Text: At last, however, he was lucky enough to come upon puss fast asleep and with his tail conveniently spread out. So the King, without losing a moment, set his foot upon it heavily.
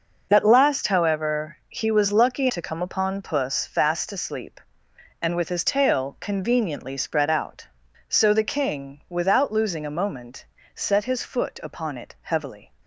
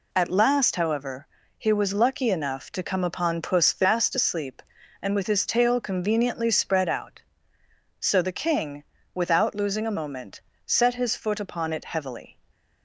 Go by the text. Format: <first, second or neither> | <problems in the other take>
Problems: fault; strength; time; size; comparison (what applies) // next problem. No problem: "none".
second | skips "enough"; at 2.5 s